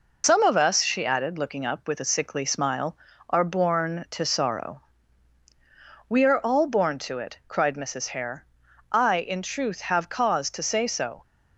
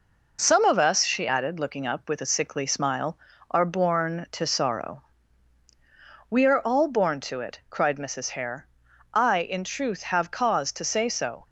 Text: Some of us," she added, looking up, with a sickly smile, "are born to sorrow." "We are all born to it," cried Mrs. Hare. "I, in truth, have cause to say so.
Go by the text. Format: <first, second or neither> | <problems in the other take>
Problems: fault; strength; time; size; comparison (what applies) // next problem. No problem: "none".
second | loses the start of "Some"; at 0.2 s; 75 ms